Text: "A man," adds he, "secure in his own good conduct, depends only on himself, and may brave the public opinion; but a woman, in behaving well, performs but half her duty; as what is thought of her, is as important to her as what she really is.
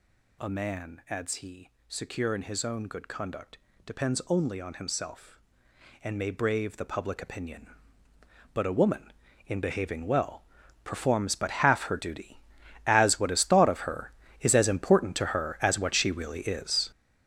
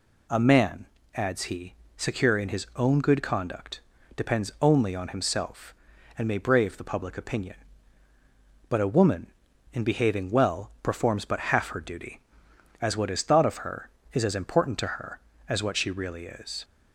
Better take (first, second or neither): second